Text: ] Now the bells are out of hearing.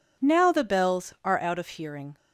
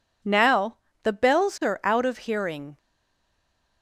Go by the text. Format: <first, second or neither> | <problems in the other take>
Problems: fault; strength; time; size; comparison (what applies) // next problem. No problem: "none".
first | pauses between "Now" and "the"; slight; at 0.7 s; 0.26 s long // stays silent after the last word; from 2.7 s on; 1.1 s long